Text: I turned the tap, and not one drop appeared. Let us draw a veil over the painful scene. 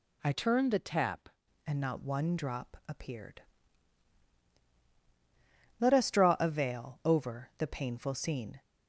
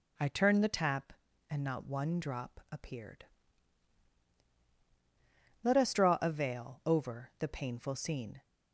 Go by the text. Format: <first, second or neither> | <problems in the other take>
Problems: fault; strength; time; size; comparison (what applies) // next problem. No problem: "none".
second | changes voice from "turned" to "tap"; from 0.3 to 1.2 s; 0.9 s long